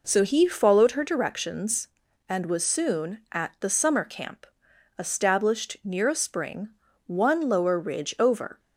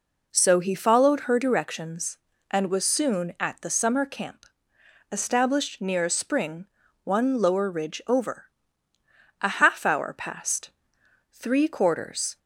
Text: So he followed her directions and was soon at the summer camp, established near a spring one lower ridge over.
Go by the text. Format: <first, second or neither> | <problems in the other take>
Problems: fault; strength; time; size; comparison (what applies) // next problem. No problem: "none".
first | pauses between "spring" and "one"; at 6.6 s; 0.38 s long; also in the first // goes on to say "A half hour passed three quarters"; strong; from 9.4 s on; 2.9 s long